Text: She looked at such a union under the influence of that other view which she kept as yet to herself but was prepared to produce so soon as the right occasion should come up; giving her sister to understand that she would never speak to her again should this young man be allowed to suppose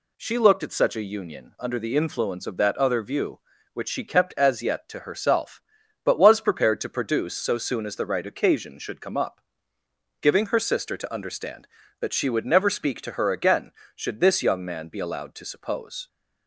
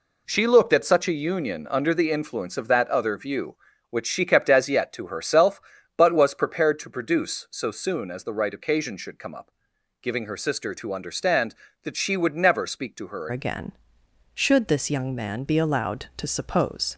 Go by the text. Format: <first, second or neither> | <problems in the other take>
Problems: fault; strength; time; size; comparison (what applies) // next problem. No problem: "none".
first | changes voice at "again"; from 13.3 s on; 3.6 s long